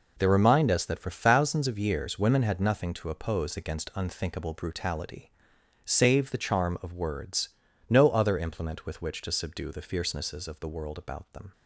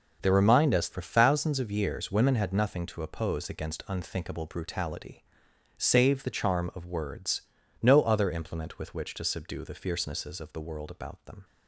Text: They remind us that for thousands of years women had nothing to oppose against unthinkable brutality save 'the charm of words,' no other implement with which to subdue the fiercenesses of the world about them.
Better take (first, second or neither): first